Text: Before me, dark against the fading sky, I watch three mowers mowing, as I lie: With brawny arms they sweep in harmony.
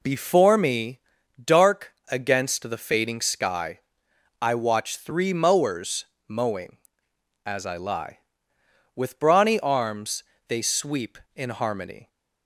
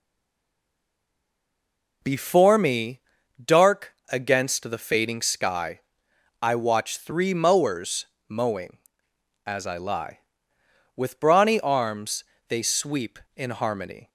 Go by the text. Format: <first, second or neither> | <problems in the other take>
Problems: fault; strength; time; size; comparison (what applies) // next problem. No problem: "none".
first | stays silent before the first word; noticeable; until 2.0 s; 2.0 s long // pauses between "dark" and "against"; slight; at 3.9 s; 0.16 s long; slight in the first // pauses between "mowers" and "mowing"; slight; at 8.0 s; 0.22 s long; slight in the first // pauses between "arms" and "they"; slight; at 12.2 s; 0.24 s long; slight in the first